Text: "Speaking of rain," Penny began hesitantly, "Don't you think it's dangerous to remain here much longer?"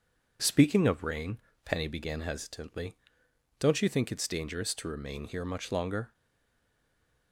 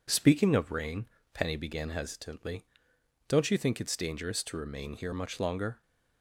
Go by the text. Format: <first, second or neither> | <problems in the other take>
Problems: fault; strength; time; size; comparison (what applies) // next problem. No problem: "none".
second | stays silent after the last word; noticeable; from 6.1 s on; 1.2 s long